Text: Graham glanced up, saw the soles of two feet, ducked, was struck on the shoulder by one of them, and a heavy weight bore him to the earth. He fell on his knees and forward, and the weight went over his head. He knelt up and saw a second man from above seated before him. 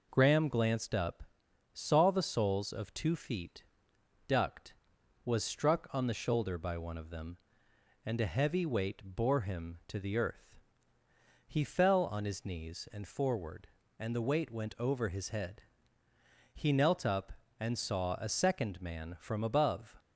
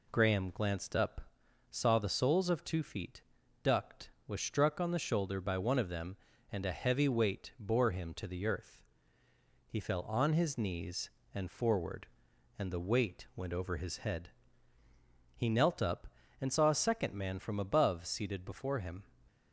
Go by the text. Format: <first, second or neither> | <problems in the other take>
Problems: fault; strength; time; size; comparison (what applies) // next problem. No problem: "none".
second | stops before "seated before him"; at 19.9 s